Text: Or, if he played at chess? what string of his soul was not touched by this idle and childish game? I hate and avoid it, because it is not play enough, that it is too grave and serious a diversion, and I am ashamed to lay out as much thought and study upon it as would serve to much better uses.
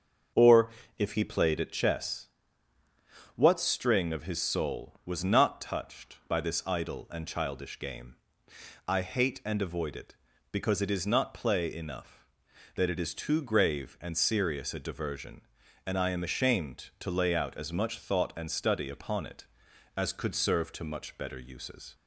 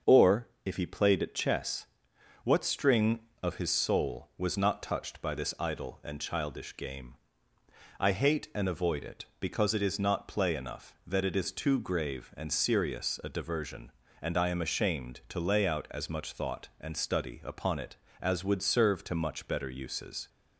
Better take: second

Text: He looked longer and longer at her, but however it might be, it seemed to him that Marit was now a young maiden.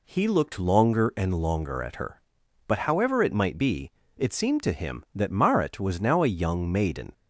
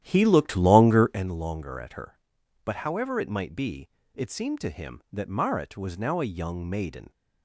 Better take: first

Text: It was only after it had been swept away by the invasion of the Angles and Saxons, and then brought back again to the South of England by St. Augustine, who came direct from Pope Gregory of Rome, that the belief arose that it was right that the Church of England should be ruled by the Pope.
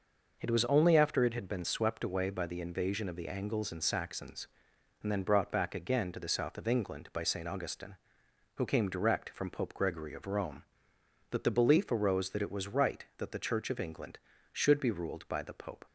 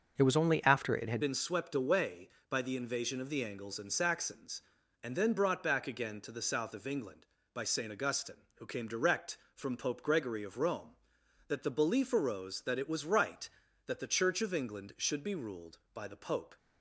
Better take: first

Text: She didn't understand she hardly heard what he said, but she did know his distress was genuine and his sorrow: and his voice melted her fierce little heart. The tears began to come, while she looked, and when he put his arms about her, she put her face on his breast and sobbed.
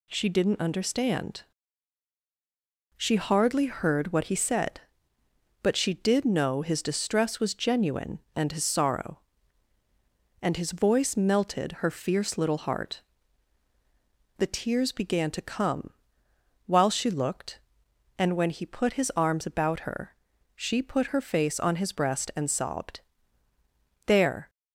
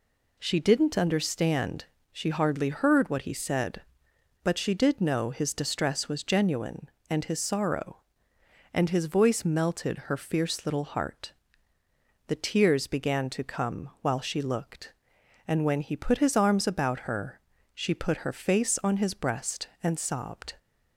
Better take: second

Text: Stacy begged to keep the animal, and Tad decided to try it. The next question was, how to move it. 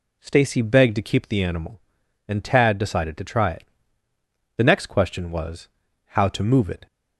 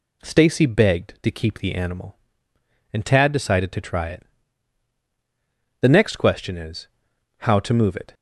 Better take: first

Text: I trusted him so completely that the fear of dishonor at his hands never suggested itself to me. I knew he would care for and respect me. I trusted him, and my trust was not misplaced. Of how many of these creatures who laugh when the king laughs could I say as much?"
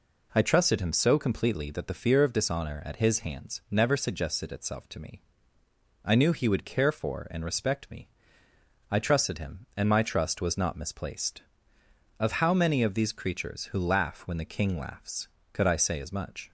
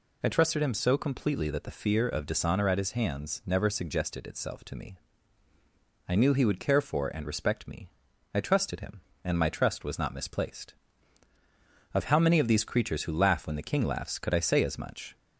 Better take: neither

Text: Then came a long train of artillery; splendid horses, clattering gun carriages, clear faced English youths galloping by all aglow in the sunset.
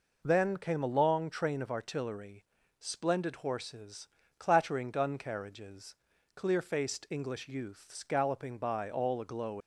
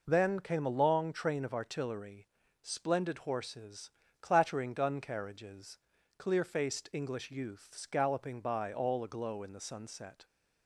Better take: second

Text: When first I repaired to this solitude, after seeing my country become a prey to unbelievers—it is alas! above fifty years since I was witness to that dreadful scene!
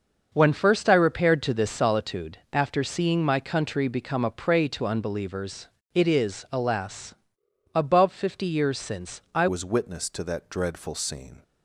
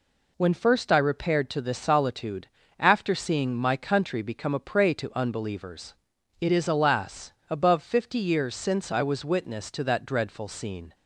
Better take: second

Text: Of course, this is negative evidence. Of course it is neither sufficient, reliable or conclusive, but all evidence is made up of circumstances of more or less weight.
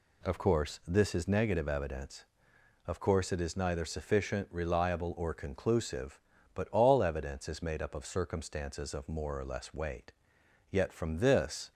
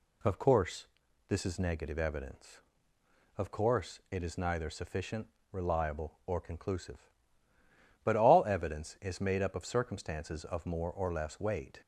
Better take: second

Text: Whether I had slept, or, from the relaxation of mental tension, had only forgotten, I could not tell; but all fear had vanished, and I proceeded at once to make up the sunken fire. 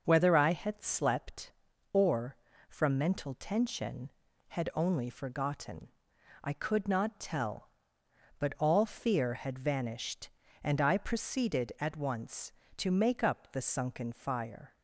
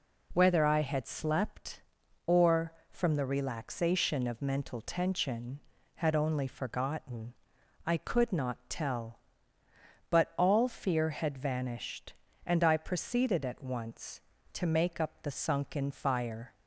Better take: second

